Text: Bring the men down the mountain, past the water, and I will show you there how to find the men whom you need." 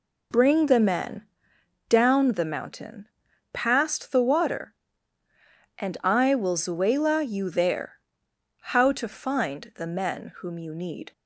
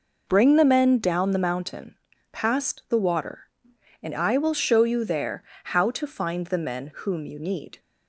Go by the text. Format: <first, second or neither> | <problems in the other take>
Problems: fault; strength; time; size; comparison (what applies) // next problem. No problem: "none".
second | pauses between "men" and "down"; noticeable; at 1.2 s; 0.64 s long // says "zuela" for "show"; at 6.5 s // pauses between "there" and "how"; noticeable; at 7.9 s; 0.72 s long; slight in the second